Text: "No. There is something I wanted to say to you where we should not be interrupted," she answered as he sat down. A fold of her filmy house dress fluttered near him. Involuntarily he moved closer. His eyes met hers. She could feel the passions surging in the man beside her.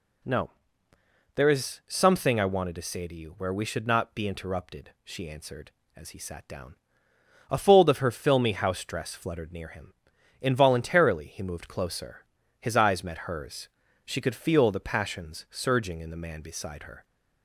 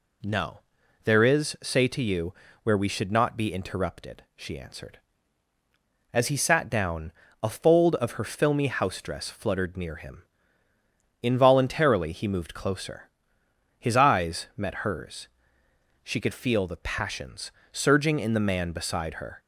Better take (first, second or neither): first